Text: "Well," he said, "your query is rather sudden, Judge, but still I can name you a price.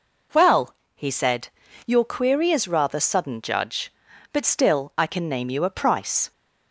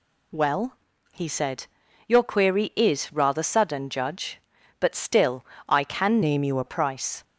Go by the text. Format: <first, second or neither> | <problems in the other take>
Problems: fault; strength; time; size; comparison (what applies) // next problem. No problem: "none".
first | pauses between "still" and "I"; slight; at 5.4 s; 0.24 s long // changes voice from "name" to "a"; from 6.2 to 6.6 s; 0.4 s long